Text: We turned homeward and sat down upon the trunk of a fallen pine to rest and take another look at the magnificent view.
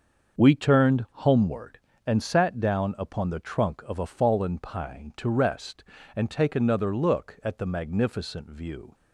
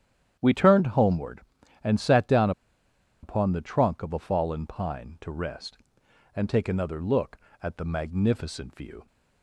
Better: first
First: starts louder than the rest; until 1.4 s; 6.5 dB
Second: starts louder than the rest; strong; until 1.4 s; 10 dB // pauses between "down" and "upon"; noticeable; at 2.5 s; 0.71 s long

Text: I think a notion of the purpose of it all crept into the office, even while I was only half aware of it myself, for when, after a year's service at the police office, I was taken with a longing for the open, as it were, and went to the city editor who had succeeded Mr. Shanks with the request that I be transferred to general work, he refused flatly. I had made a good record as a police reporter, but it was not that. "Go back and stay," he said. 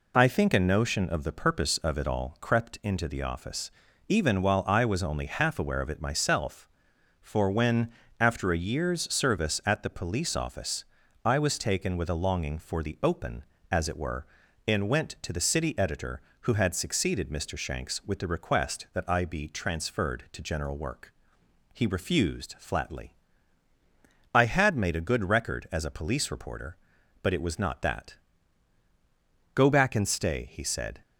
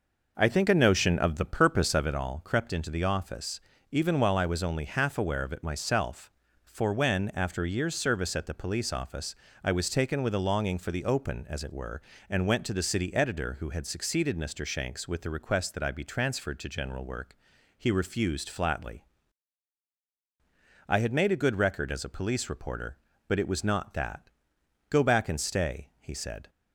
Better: first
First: none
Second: starts louder than the rest; noticeable; until 2.2 s; 5.5 dB

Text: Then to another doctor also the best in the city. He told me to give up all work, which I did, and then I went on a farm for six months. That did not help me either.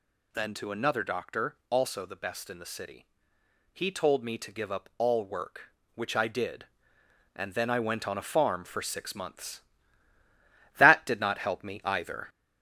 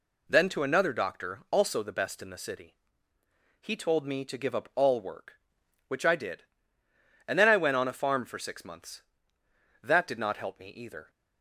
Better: second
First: gets louder; throughout; 3.5 dB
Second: none

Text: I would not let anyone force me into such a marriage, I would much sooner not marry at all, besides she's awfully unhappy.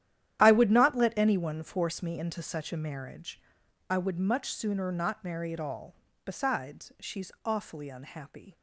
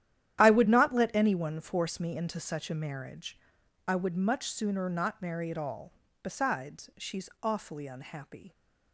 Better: neither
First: starts louder than the rest; strong; until 1.4 s; 11 dB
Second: starts louder than the rest; strong; until 1.4 s; 11 dB

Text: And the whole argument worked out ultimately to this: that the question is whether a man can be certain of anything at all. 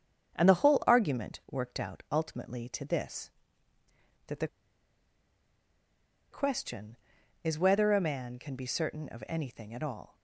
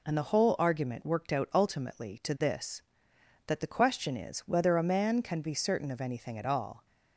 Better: second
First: starts louder than the rest; strong; until 1.3 s; 7.5 dB // pauses between "the" and "question"; strong; at 4.4 s; 1.8 s long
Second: none

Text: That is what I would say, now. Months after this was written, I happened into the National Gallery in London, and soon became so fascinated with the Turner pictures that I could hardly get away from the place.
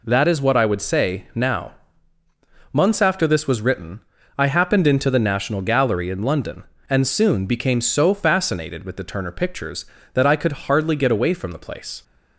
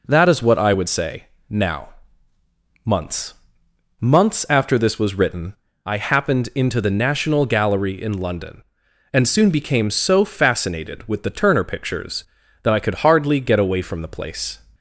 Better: first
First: none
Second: says "Months" twice; at 4.0 s

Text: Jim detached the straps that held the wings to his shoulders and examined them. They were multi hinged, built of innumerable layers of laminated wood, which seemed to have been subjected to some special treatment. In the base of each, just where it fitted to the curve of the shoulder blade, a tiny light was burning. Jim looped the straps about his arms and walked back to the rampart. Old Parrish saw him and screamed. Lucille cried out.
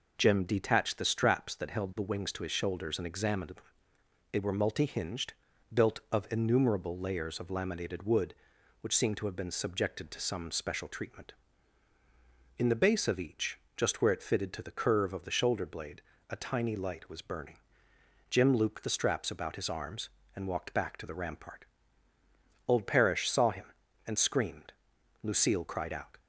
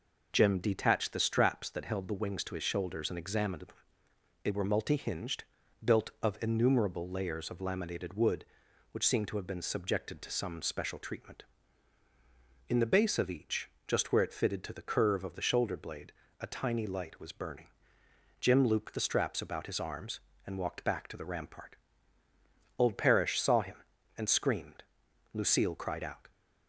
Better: neither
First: none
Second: none

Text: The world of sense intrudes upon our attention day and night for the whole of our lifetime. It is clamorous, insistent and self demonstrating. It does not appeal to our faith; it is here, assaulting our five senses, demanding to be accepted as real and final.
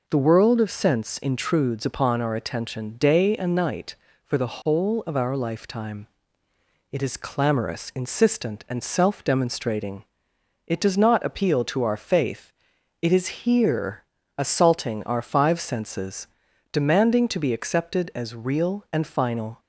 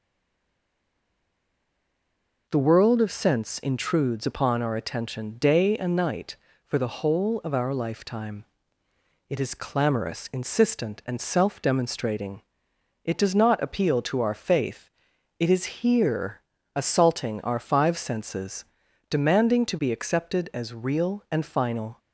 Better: first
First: none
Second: stays silent before the first word; until 2.4 s; 2.4 s long

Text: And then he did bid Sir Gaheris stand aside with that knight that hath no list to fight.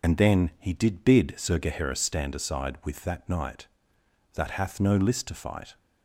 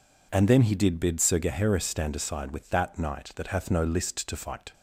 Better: second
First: loses the start of "And"; at 0.0 s; 55 ms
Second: none

